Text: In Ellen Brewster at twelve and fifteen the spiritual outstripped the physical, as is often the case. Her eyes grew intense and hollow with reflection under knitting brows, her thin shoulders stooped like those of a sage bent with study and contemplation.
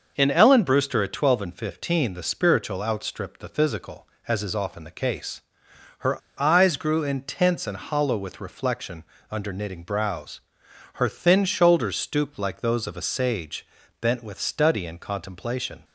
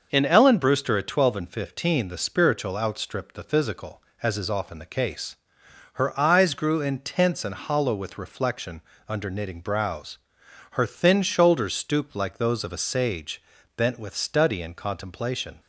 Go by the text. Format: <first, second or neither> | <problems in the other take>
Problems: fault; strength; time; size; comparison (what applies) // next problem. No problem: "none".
second | starts louder than the rest; noticeable; until 1.1 s; 6 dB; noticeable in the second // pauses between "Her" and "eyes"; slight; at 6.1 s; 0.22 s long // pauses between "reflection" and "under"; slight; at 9.0 s; 0.26 s long; slight in the second // pauses between "sage" and "bent"; slight; at 13.6 s; 0.34 s long; slight in the second